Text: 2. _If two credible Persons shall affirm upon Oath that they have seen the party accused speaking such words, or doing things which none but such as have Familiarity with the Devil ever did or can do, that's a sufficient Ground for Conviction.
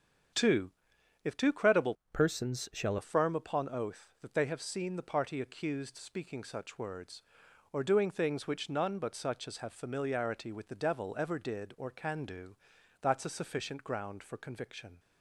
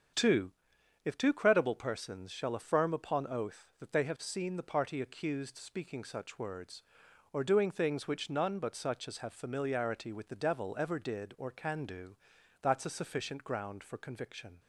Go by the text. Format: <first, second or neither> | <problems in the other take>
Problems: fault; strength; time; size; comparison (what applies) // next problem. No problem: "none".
second | starts louder than the rest; strong; until 1.8 s; 7.5 dB; strong in the second // changes voice from "Persons" to "shall"; from 2.1 to 2.9 s; 0.8 s long